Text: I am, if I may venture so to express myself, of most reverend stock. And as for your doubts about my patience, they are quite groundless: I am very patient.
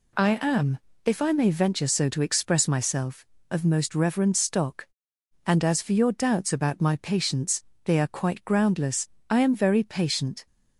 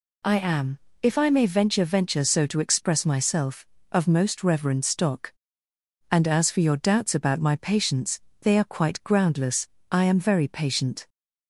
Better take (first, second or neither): first